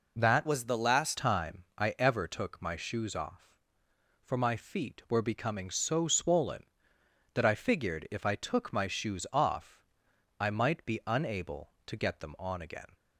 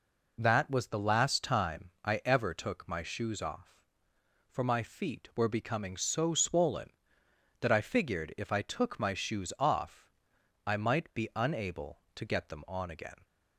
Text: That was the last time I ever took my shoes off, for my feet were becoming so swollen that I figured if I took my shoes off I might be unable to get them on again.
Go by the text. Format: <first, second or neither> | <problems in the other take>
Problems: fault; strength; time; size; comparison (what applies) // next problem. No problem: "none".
second | changes voice from "was" to "last"; from 0.4 to 1.1 s; 0.7 s long // pauses between "time" and "I"; slight; at 1.6 s; 0.16 s long; slight in the second // pauses between "off" and "I"; noticeable; at 9.8 s; 0.56 s long; noticeable in the second